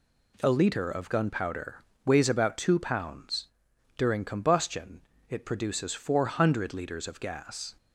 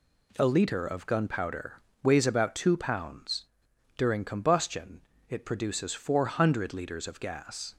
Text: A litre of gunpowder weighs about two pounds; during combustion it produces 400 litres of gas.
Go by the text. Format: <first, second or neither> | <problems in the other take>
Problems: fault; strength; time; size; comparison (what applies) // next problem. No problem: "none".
neither | pauses between "gunpowder" and "weighs"; slight; the same in both // pauses between "combustion" and "it"; slight; the same in both